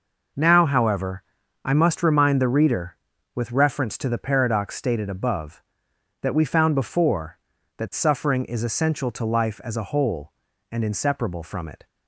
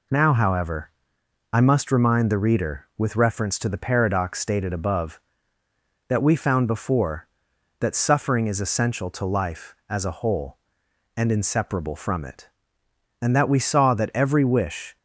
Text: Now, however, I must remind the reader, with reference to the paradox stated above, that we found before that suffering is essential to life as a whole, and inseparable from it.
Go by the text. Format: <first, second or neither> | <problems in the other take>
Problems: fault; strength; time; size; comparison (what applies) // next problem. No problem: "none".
first | goes on to say "And that we saw that every wish"; strong; from 13.2 s on; 1.7 s long